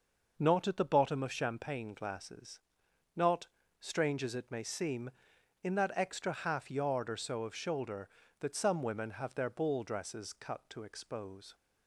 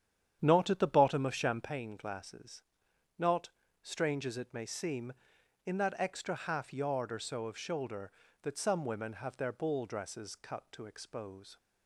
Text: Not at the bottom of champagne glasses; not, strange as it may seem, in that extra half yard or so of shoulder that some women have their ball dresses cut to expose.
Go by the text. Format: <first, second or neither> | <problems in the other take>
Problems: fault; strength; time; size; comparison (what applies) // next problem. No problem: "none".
first | starts louder than the rest; strong; until 1.8 s; 9.5 dB